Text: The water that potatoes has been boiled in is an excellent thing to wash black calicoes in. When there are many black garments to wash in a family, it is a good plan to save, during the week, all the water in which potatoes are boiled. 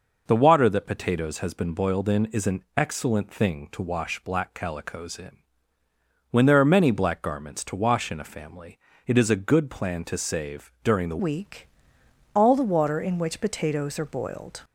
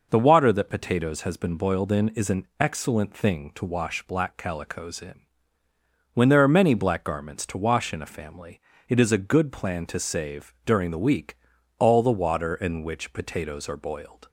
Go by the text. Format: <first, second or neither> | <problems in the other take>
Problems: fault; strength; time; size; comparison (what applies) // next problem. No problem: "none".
second | changes voice at "week"; from 11.1 s on; 3.5 s long